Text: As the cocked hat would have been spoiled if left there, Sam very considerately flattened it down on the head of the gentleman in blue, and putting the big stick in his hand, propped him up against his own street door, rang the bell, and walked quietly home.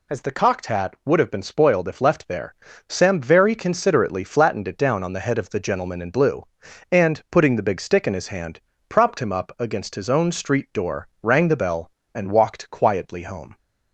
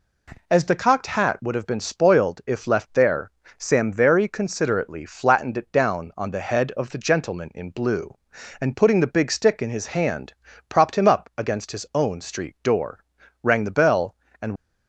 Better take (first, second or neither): first